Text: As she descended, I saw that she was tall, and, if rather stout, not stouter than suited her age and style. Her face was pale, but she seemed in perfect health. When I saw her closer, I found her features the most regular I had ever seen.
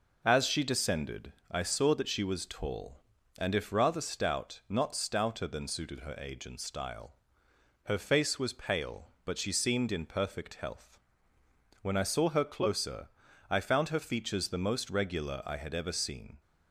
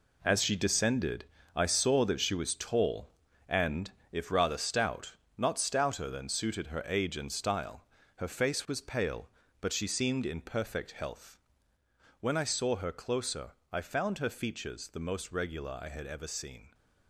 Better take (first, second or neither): first